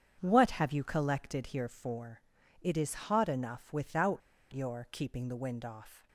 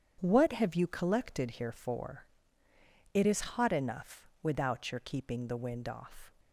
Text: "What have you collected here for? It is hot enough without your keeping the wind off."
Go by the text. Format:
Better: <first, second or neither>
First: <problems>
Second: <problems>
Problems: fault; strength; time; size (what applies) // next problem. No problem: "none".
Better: second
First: starts louder than the rest; strong; until 1.2 s; 8 dB // pauses between "without" and "your"; slight; at 4.2 s; 0.31 s long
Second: starts louder than the rest; strong; until 1.2 s; 8 dB